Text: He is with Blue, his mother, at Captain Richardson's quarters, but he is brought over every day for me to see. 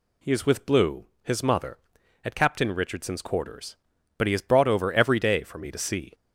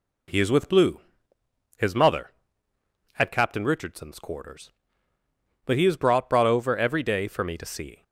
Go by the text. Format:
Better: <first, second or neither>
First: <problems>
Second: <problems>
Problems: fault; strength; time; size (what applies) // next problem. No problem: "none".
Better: first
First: none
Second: says "brought" twice; at 6.2 s